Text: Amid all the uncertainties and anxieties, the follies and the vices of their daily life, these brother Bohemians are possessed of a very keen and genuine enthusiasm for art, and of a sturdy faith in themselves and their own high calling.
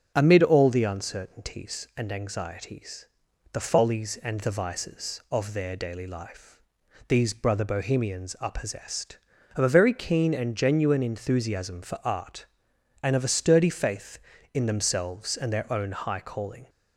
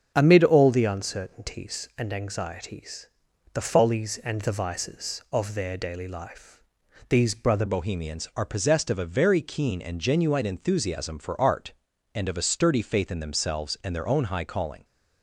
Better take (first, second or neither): first